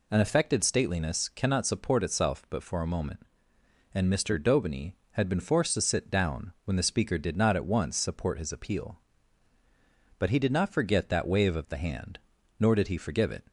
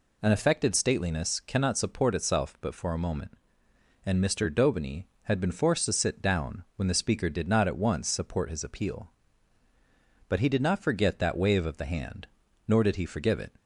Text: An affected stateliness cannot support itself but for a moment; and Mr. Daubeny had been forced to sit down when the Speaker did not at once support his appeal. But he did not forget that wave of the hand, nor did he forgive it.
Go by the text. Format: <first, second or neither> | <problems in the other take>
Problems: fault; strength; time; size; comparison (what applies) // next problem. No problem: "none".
neither | none